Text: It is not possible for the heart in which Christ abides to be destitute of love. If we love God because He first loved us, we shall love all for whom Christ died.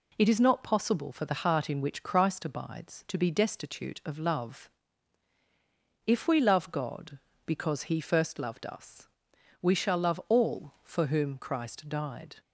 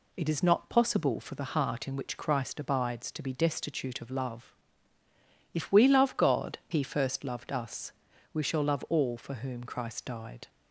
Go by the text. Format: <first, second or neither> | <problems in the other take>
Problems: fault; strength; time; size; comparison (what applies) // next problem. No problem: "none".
first | skips "because"; at 6.6 s